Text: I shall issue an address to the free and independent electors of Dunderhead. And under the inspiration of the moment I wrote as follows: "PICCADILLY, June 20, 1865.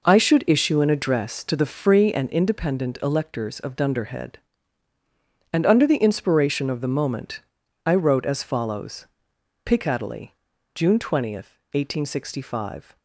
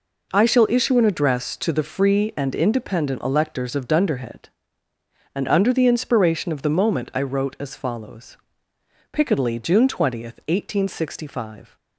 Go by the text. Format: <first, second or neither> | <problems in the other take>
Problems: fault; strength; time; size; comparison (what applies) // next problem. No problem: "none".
second | says "should" for "shall"; at 0.1 s // pauses between "moment" and "I"; noticeable; at 7.3 s; 0.46 s long